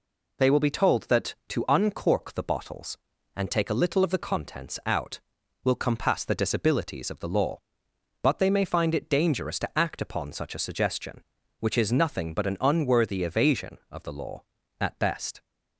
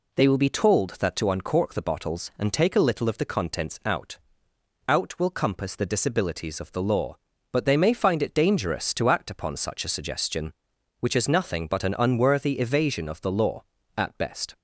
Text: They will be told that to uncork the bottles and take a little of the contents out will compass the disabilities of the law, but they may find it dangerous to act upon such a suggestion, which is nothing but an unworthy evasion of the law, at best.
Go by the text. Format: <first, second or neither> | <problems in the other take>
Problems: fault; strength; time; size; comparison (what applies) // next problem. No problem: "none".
first | says "out" twice; at 4.8 s